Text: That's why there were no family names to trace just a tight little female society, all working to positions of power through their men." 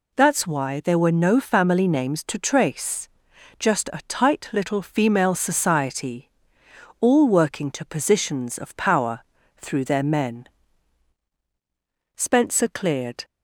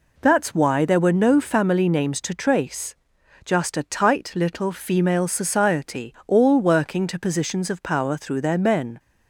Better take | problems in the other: second | pauses between "trace" and "just"; noticeable; at 3.0 s; 0.50 s long; noticeable in the second // pauses between "power" and "through"; slight; at 9.2 s; 0.36 s long // goes on to say "Spencer cleared"; noticeable; from 12.1 s on; 1.0 s long

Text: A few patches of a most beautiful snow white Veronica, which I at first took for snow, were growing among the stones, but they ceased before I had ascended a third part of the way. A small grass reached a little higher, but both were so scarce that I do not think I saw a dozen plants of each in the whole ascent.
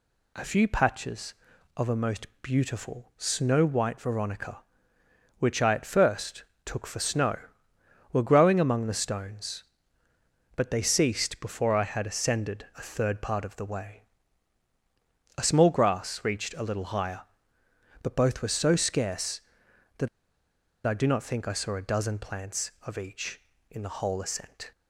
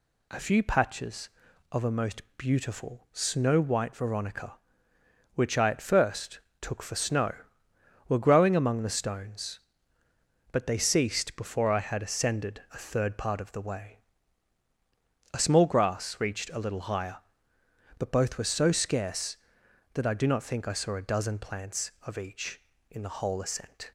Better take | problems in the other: second | pauses between "most" and "beautiful"; slight; at 2.2 s; 0.16 s long; slight in the second // pauses between "first" and "took"; slight; at 6.4 s; 0.22 s long; slight in the second // pauses between "that" and "I"; noticeable; at 20.0 s; 0.78 s long

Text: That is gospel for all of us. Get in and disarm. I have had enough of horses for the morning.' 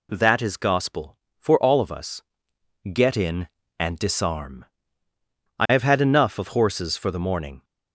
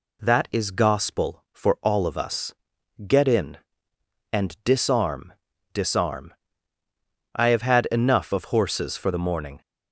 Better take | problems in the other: first | says "disarm" twice; at 5.7 s

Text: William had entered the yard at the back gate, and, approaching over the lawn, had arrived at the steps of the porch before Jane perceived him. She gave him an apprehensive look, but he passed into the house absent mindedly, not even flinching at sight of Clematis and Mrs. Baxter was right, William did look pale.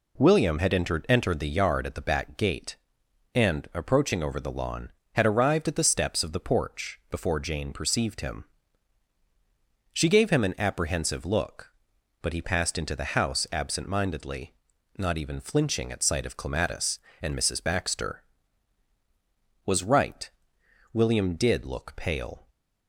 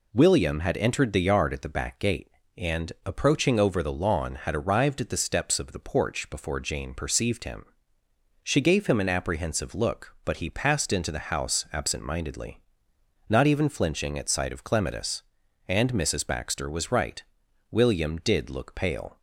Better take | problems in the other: second | says "entered" twice; at 1.0 s

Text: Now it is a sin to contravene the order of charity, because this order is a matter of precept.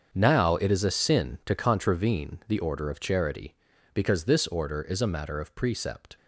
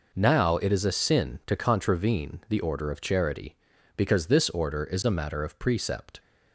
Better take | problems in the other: second | gets quieter; strong; throughout; 14 dB

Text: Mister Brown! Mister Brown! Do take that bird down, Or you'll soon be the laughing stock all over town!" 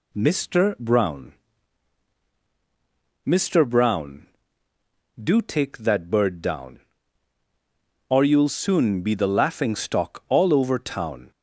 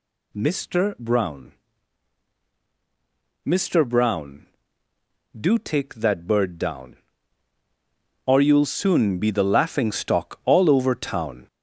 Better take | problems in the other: first | gets louder; noticeable; throughout; 5 dB

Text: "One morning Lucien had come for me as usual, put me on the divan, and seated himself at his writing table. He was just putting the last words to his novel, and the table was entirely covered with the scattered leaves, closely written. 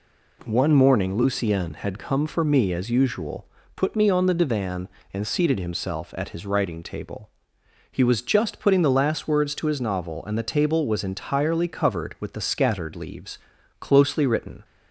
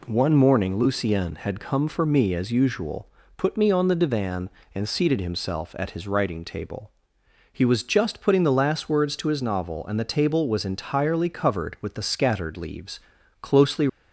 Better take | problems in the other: first | stops before "written"; at 13.8 s

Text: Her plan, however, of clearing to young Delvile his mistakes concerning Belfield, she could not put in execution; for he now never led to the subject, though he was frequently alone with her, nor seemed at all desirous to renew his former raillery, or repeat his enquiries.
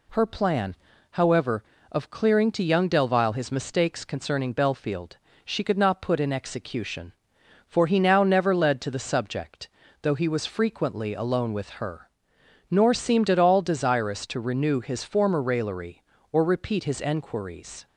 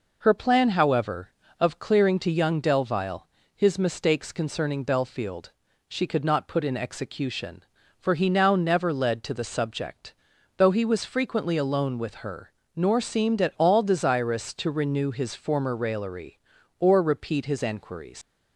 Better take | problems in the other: first | pauses between "Delvile" and "his"; slight; at 3.2 s; 0.26 s long // leaves "enquiries" unfinished; at 18.2 s; 110 ms

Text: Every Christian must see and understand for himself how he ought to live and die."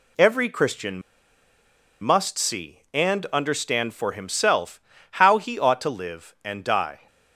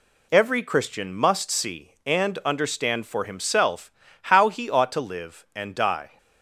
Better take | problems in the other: second | pauses between "Christian" and "must"; at 1.0 s; 1.0 s long // pauses between "himself" and "how"; slight; at 4.8 s; 0.32 s long; slight in the second

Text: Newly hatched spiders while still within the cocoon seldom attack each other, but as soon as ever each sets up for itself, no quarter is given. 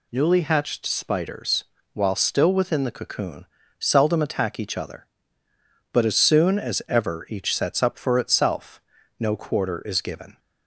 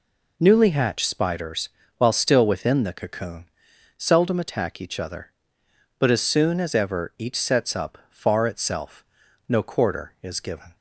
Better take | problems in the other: first | pauses between "spiders" and "while"; slight; at 1.6 s; 0.26 s long; slight in the first // pauses between "cocoon" and "seldom"; noticeable; at 3.4 s; 0.50 s long; slight in the first // says "far" for "for"; at 8.0 s

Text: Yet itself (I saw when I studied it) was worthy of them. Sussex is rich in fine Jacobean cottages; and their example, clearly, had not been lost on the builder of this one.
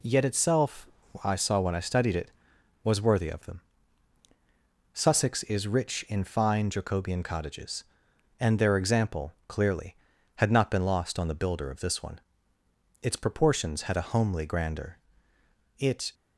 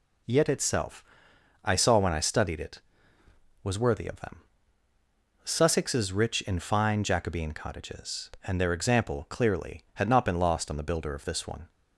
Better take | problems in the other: second | goes on to say "Its proportions had a homely grandeur It"; strong; from 13.0 s on; 3.1 s long

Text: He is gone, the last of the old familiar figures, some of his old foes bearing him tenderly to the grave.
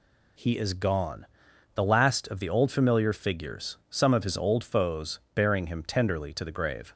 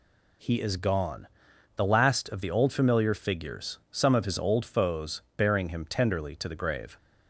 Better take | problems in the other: neither | pauses between "foes" and "bearing"; slight; the same in both

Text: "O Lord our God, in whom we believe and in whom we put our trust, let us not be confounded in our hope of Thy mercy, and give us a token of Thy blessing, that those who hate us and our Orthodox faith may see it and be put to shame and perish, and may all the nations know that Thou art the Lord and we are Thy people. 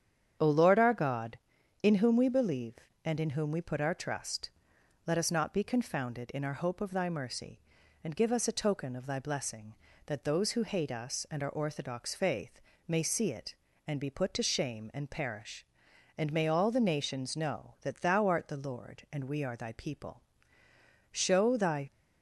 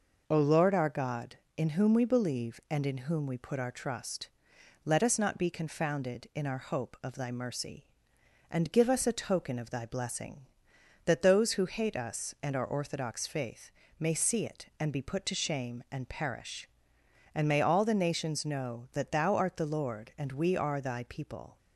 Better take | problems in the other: second | starts louder than the rest; strong; until 1.8 s; 8.5 dB // pauses between "faith" and "may"; slight; at 12.6 s; 0.28 s long; slight in the second // goes on to say "Show Thy"; noticeable; from 21.1 s on; 0.78 s long

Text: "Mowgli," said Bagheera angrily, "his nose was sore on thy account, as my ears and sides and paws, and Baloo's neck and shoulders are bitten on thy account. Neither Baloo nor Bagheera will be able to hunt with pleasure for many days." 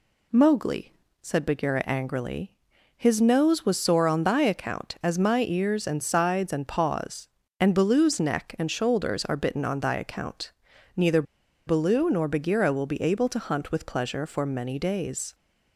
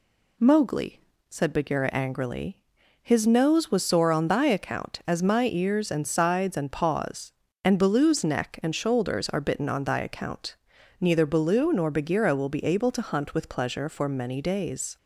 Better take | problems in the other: second | pauses between "Neither" and "Baloo"; at 11.2 s; 0.43 s long

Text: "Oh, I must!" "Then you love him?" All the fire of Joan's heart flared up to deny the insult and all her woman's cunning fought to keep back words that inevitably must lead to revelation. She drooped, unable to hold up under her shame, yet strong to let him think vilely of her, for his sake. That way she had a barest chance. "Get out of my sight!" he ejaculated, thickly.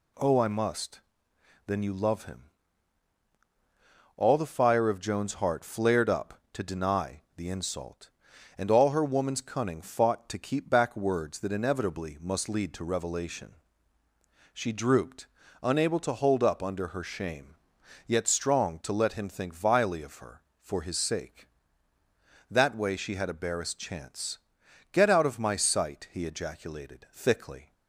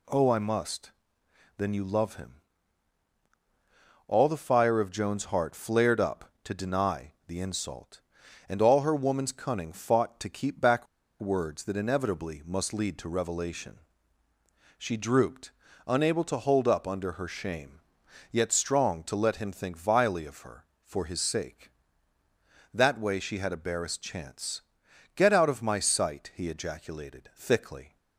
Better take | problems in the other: first | pauses between "back" and "words"; slight; at 10.8 s; 0.34 s long

